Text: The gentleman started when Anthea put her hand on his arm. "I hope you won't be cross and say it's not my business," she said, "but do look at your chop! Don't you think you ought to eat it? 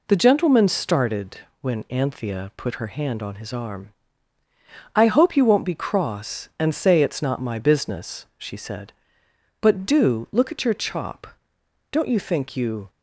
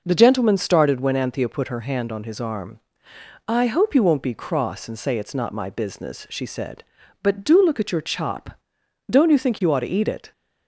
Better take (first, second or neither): second